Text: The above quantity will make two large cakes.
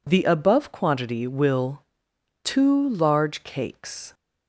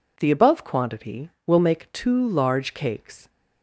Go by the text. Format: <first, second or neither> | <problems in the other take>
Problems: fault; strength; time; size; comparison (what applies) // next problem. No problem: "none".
second | skips "make"; at 2.1 s